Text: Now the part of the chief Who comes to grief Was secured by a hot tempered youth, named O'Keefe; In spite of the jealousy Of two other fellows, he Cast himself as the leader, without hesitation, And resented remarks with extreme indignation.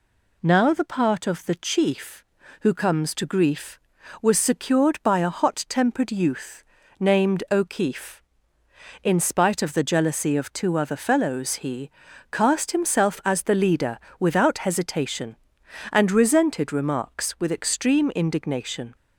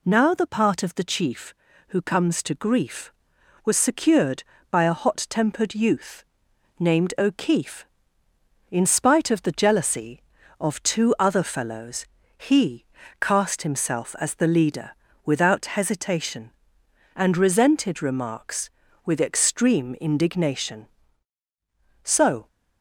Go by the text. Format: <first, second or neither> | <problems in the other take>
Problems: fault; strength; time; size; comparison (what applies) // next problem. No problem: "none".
first | pauses between "he" and "Cast"; slight; at 12.8 s; 0.36 s long; also in the first // goes on to say "So"; slight; from 22.0 s on; 0.44 s long